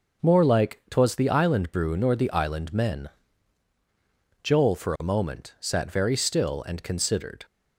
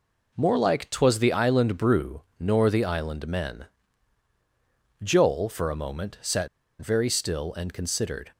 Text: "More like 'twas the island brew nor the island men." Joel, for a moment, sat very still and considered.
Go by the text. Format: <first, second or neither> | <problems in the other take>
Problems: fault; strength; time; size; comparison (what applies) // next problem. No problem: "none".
first | pauses between "brew" and "nor"; slight; at 2.2 s; 0.16 s long // pauses between "sat" and "very"; slight; at 6.4 s; 0.31 s long